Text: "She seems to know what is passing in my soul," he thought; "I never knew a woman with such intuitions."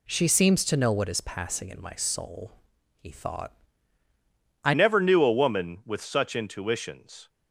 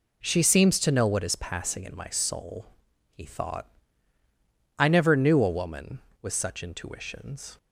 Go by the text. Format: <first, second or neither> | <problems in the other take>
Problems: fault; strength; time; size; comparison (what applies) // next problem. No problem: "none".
second | changes voice at "never"; from 4.7 s on; 2.5 s long